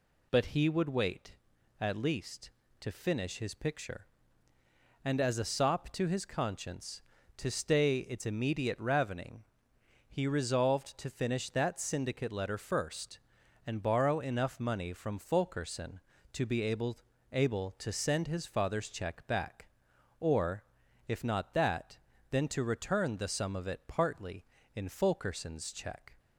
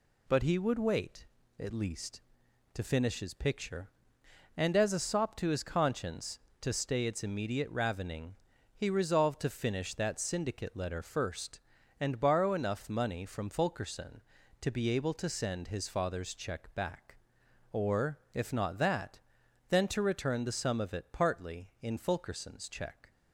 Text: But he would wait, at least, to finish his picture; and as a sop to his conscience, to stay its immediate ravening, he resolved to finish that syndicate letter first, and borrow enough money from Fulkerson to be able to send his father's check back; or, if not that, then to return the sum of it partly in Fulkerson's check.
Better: second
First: says "able" twice; at 17.3 s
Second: none

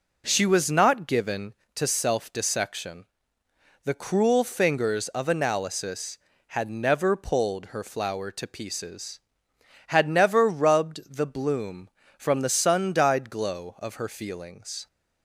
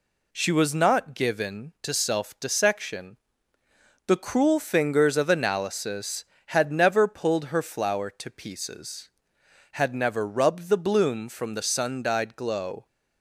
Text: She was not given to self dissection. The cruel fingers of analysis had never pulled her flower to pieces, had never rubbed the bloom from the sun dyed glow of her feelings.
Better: first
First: none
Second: stops before "of her feelings"; at 12.8 s

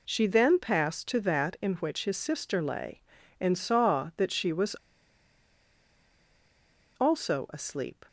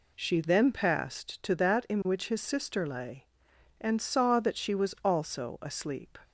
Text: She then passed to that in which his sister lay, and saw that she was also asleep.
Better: second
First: pauses between "was" and "also"; strong; at 4.7 s; 2.2 s long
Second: none

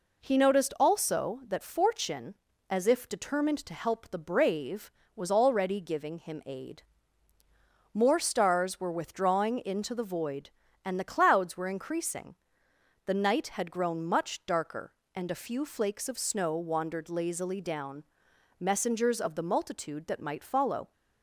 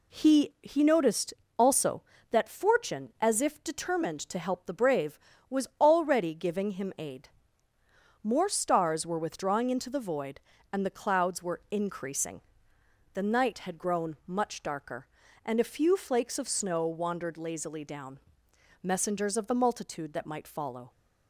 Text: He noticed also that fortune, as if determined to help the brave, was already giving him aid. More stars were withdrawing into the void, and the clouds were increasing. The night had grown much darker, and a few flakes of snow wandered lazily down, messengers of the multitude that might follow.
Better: first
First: none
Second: says "He" twice; at 0.6 s // pauses between "noticed" and "also"; slight; at 1.3 s; 0.24 s long

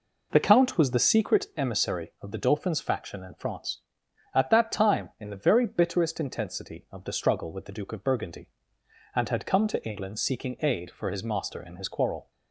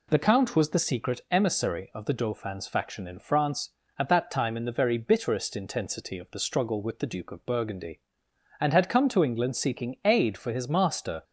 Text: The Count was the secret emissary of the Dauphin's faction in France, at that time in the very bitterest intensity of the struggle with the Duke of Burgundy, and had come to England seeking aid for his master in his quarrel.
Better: first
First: none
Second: stops before "in his quarrel"; at 11.2 s

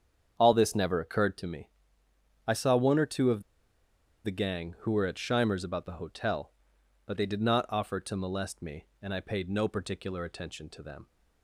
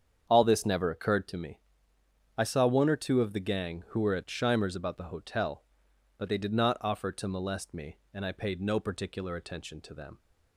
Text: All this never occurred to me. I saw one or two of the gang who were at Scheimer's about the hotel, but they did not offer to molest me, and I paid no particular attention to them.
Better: second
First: starts louder than the rest; strong; until 1.4 s; 8 dB // pauses between "of" and "the"; noticeable; at 3.4 s; 0.81 s long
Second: starts louder than the rest; strong; until 1.3 s; 8 dB

